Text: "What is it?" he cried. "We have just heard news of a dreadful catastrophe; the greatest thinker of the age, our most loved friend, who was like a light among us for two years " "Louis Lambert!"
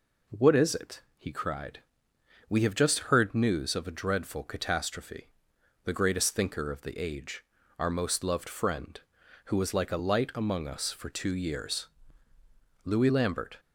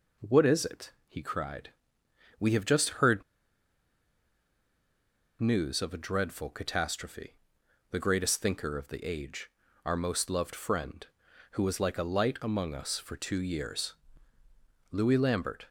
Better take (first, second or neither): first